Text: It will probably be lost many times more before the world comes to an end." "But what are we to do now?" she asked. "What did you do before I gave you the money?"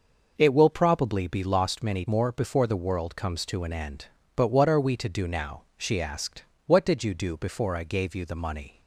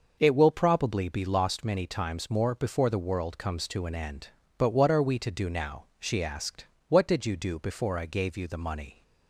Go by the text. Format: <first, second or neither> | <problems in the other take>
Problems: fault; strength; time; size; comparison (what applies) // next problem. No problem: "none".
second | skips "times"; at 2.0 s